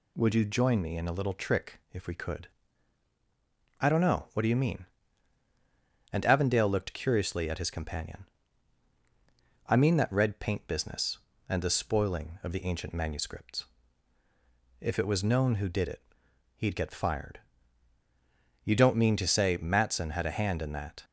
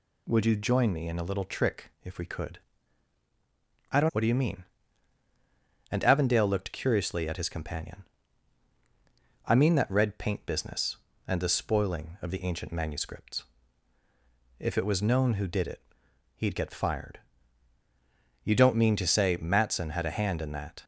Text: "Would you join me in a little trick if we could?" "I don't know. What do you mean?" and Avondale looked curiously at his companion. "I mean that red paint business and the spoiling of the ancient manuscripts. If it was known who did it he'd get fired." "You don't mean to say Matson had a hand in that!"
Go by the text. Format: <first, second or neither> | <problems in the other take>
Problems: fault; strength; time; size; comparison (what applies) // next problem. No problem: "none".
first | skips "know"; at 4.1 s // pauses between "it" and "he'd"; noticeable; at 15.8 s; 0.54 s long; noticeable in the first